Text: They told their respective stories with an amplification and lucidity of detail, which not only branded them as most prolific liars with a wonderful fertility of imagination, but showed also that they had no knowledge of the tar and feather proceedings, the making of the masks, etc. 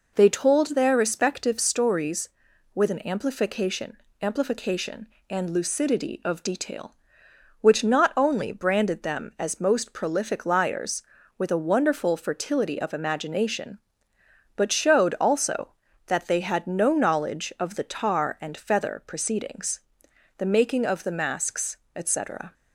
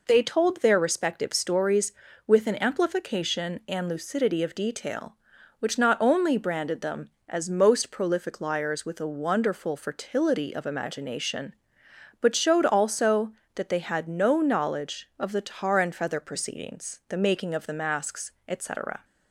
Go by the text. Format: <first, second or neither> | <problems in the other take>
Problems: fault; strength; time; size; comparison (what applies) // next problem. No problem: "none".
second | says "amplification" twice; at 4.2 s